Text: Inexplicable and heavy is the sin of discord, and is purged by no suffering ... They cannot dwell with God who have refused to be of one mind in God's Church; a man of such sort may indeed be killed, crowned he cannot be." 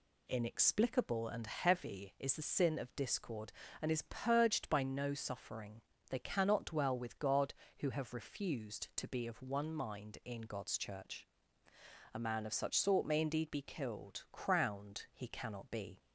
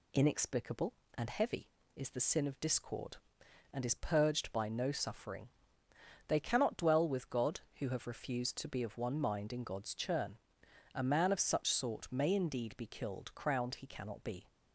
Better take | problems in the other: first | says "Churn" for "Church"; at 9.9 s

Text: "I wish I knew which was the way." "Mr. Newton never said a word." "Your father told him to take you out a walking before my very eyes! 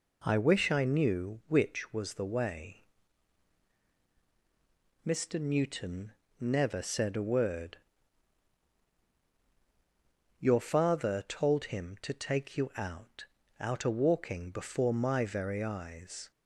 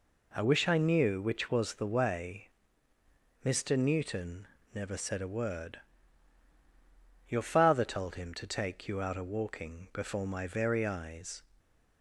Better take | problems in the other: second | pauses between "Newton" and "never"; slight; at 6.1 s; 0.26 s long; slight in the second // says "out" twice; at 13.5 s

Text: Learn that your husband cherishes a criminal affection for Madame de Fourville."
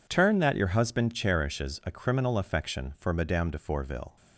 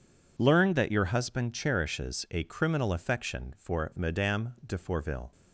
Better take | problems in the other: second | says "Turn" for "Learn"; at 0.0 s

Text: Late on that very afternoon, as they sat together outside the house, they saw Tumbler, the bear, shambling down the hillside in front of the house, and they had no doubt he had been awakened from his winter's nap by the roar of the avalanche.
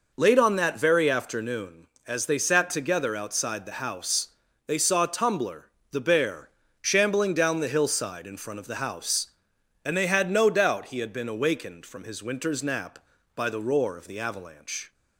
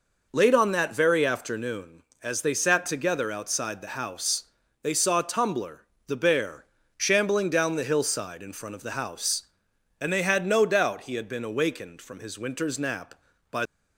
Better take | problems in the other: first | stops before "the roar of the avalanche"; at 13.6 s

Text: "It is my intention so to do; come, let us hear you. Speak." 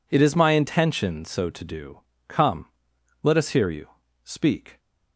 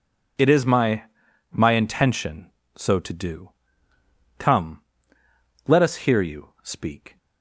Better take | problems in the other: first | says "my" twice; at 1.5 s

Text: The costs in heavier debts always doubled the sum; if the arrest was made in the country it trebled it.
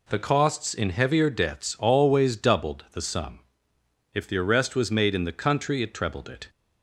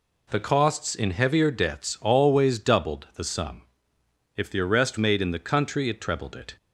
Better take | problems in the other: first | skips "was"; at 4.9 s

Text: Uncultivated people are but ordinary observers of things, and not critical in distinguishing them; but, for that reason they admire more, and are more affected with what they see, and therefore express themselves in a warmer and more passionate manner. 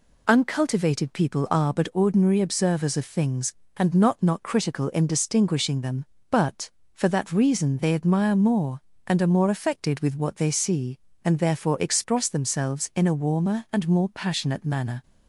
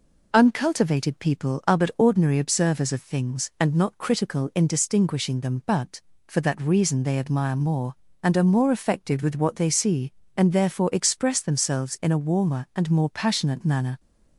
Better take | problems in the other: second | says "not" twice; at 4.2 s

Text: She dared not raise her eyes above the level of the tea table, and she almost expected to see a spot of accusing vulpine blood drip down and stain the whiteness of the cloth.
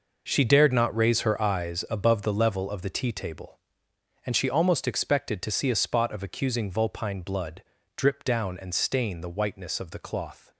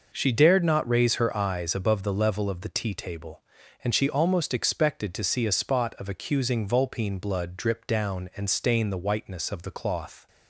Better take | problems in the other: second | gets quieter; strong; throughout; 11.5 dB // pauses between "blood" and "drip"; slight; at 7.6 s; 0.32 s long

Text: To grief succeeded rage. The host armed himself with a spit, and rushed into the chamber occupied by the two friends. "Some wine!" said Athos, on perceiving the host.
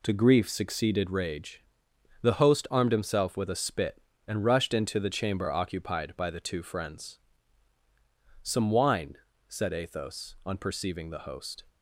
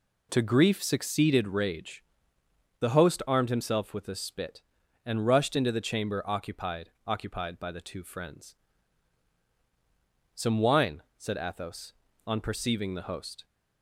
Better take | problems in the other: first | says "occupied" twice; at 7.0 s

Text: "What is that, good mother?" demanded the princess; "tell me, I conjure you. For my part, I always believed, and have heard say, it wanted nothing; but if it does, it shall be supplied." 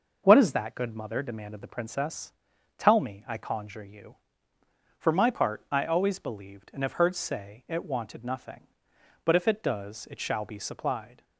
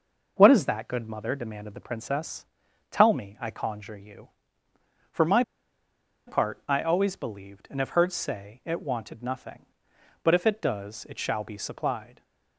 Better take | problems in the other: first | pauses between "my" and "part"; noticeable; at 5.4 s; 0.85 s long

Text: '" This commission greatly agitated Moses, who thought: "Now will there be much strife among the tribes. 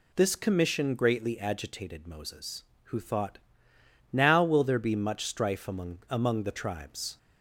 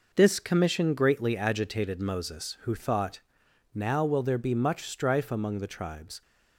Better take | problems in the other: second | says "among" twice; at 6.0 s

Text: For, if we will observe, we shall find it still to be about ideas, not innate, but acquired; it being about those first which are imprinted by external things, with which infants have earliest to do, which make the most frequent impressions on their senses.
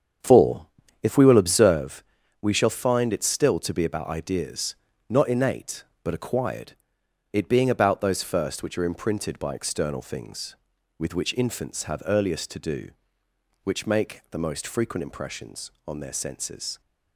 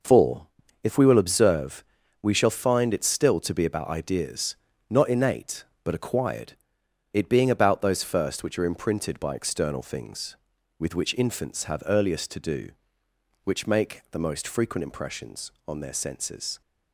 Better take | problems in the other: second | starts louder than the rest; strong; until 1.9 s; 7.5 dB

